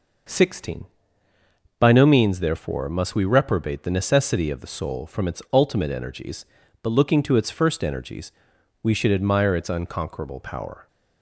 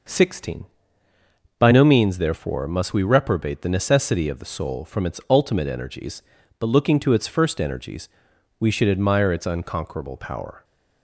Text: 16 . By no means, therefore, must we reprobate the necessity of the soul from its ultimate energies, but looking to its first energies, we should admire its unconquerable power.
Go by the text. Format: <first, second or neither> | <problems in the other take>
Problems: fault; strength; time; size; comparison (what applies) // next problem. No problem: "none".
neither | none